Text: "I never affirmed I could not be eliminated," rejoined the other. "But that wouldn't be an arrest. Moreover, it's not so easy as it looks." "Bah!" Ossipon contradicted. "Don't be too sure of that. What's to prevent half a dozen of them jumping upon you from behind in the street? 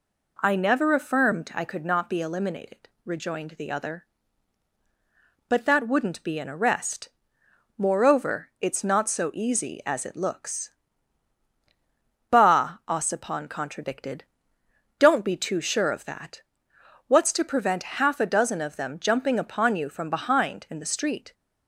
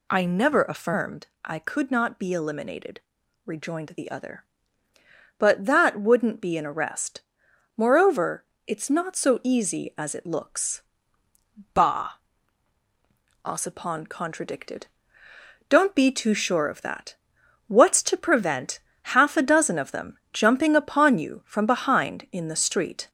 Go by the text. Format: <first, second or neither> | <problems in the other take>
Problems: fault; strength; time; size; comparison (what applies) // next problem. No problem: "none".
first | gets louder; slight; throughout; 3 dB // pauses between "affirmed" and "I"; slight; at 1.2 s; 0.16 s long // pauses between "prevent" and "half"; slight; at 18.7 s; 0.34 s long